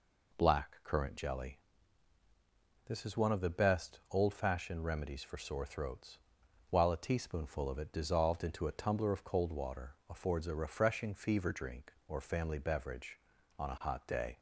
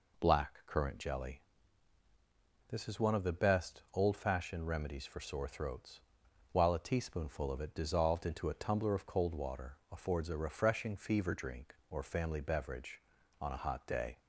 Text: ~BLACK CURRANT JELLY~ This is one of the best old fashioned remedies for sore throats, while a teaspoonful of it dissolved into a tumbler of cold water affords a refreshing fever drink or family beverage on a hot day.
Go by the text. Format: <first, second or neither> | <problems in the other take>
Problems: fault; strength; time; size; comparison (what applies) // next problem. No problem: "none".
neither | none